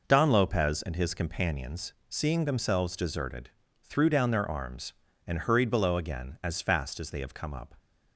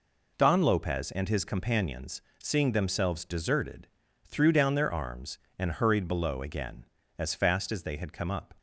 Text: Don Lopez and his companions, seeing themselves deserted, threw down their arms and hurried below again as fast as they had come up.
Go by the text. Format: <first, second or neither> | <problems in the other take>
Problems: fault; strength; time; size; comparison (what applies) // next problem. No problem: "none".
second | says "have" for "had"; at 7.1 s